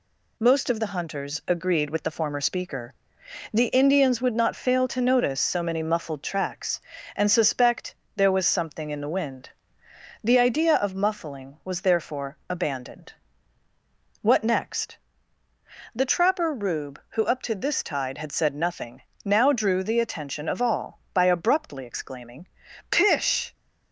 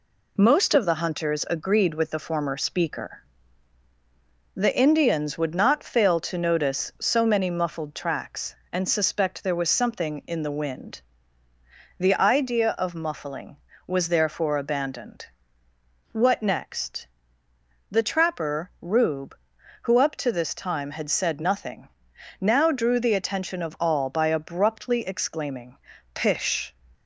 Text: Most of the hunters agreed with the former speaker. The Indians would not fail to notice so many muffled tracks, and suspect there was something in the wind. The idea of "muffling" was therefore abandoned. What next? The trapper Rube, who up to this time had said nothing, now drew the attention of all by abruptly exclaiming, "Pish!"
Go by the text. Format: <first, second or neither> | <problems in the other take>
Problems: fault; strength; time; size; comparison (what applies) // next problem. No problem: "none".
second | pauses between "suspect" and "there"; slight; at 7.9 s; 0.22 s long // says "tide" for "time"; at 17.8 s